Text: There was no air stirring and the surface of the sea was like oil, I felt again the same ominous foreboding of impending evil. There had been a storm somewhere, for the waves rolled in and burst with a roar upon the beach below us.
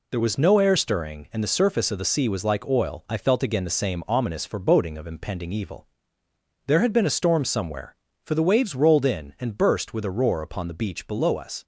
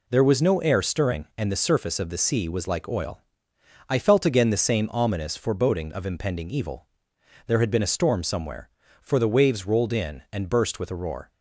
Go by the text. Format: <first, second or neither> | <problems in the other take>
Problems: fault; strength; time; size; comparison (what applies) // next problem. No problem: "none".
first | stops before "upon the beach below us"; at 11.3 s